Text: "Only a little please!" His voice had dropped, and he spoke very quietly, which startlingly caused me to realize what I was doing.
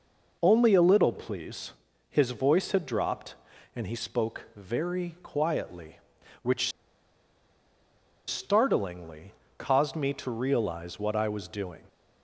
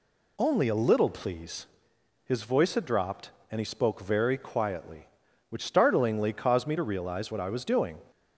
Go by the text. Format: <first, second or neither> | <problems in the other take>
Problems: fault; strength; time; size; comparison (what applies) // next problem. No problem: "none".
second | pauses between "which" and "startlingly"; strong; at 6.7 s; 1.5 s long // pauses between "startlingly" and "caused"; slight; at 9.3 s; 0.28 s long